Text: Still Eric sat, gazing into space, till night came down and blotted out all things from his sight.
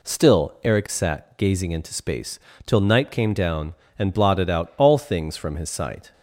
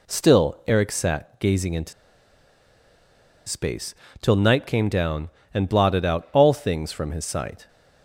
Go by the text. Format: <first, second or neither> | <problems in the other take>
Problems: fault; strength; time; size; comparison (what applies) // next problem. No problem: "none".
first | pauses between "into" and "space"; strong; at 1.9 s; 1.5 s long